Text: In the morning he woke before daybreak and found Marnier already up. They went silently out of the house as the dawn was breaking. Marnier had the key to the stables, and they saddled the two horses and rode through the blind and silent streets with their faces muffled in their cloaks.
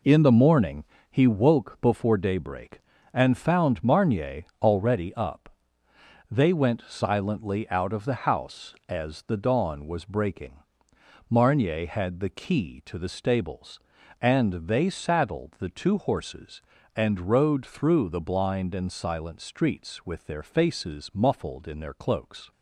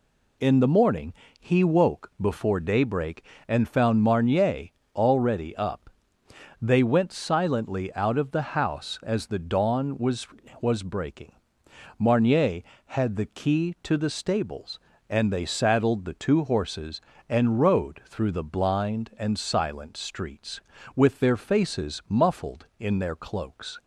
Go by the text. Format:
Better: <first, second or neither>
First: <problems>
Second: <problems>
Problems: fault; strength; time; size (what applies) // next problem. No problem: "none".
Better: first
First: pauses between "morning" and "he"; slight; at 0.8 s; 0.26 s long // pauses between "Marnier" and "already"; slight; at 4.4 s; 0.18 s long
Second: pauses between "morning" and "he"; slight; at 1.1 s; 0.26 s long // pauses between "Marnier" and "already"; slight; at 4.6 s; 0.28 s long // says "was" twice; at 10.5 s